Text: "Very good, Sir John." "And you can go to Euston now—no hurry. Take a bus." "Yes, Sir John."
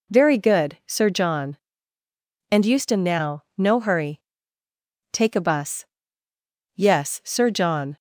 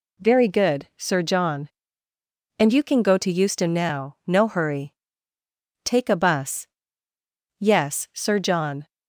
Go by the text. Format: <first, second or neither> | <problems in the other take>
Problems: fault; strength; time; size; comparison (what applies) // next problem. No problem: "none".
second | skips "you can go to"; at 2.6 s